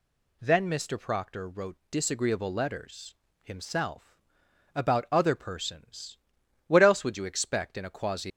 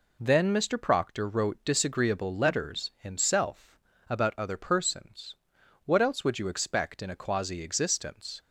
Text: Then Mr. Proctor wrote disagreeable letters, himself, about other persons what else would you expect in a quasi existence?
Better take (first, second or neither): second